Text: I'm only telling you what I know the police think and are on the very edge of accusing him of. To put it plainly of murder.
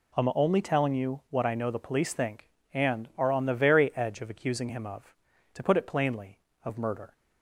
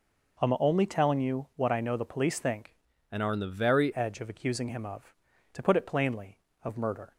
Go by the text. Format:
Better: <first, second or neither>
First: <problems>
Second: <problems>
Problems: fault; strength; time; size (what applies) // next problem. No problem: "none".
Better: first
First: none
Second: changes voice from "and" to "very"; from 3.1 to 3.9 s; 0.8 s long